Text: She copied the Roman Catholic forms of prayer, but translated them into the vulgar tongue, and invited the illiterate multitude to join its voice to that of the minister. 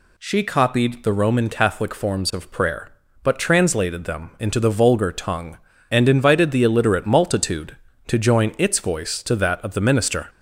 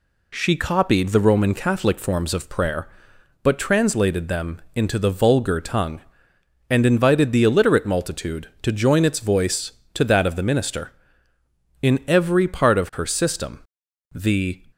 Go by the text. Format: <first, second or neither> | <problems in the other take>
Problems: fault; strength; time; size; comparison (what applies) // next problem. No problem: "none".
first | goes on to say "In every part of her system the"; strong; from 11.8 s on; 2.7 s long